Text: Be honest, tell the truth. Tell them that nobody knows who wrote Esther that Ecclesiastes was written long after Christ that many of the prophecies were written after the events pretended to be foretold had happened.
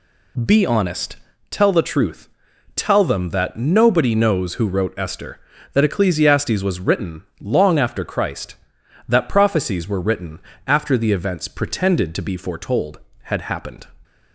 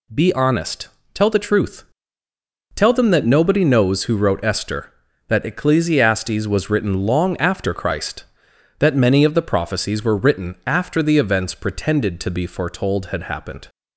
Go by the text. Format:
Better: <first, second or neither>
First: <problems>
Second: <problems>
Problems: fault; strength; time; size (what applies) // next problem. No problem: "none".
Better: second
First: pauses between "written" and "long"; slight; at 7.2 s; 0.18 s long // skips "many of the"; at 9.2 s // pauses between "written" and "after"; slight; at 10.3 s; 0.28 s long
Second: none